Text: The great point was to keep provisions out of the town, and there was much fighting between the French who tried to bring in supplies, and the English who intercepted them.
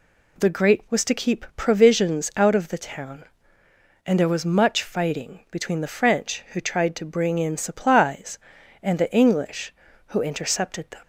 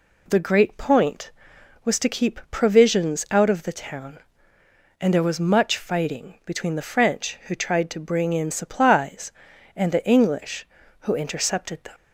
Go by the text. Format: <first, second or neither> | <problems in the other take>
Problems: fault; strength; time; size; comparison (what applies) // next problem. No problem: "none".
second | skips "point"; at 0.8 s